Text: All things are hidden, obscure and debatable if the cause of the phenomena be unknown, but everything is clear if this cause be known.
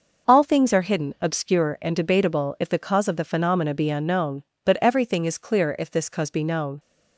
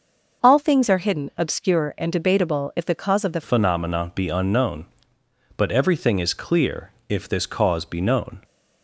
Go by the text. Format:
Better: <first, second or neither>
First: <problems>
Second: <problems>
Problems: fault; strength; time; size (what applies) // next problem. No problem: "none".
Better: first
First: none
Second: changes voice at "phenomena"; from 3.4 s on; 5.0 s long // pauses between "clear" and "if"; slight; at 6.9 s; 0.16 s long